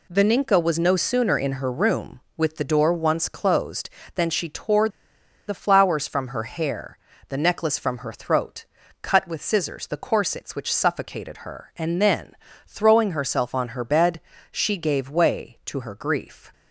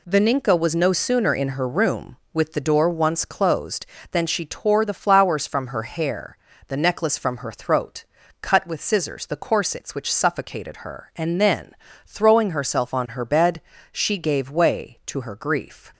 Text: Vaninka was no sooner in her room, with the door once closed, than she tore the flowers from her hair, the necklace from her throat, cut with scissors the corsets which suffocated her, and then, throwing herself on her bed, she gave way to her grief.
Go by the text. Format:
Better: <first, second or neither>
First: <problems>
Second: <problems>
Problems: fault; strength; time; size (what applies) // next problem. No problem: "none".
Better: second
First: pauses between "tore" and "the"; noticeable; at 4.8 s; 0.58 s long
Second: none